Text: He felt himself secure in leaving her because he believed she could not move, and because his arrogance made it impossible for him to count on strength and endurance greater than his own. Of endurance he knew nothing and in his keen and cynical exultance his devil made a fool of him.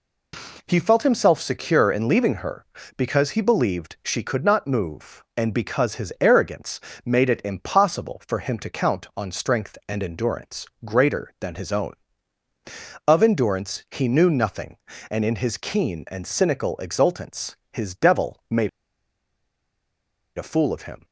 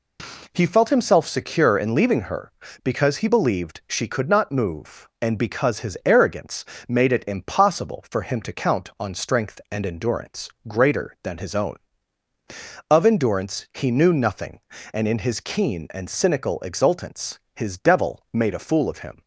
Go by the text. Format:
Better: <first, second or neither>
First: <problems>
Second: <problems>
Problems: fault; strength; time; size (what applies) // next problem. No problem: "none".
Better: second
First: pauses between "arrogance" and "made"; slight; at 6.8 s; 0.24 s long // pauses between "endurance" and "greater"; slight; at 10.6 s; 0.18 s long // pauses between "exultance" and "his"; slight; at 17.5 s; 0.16 s long // pauses between "made" and "a"; strong; at 18.6 s; 1.6 s long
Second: pauses between "arrogance" and "made"; slight; at 6.6 s; 0.22 s long // pauses between "endurance" and "greater"; slight; at 10.4 s; 0.18 s long // pauses between "exultance" and "his"; slight; at 17.3 s; 0.16 s long